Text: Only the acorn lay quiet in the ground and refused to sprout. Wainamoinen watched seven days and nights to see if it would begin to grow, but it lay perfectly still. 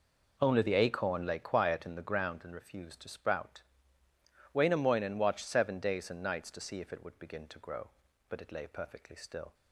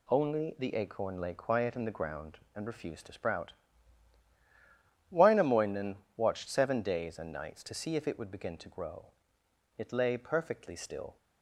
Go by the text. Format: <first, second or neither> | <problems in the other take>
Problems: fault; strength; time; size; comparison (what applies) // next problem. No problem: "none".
first | pauses between "Wainamoinen" and "watched"; slight; at 5.9 s; 0.18 s long // skips "but"; at 9.4 s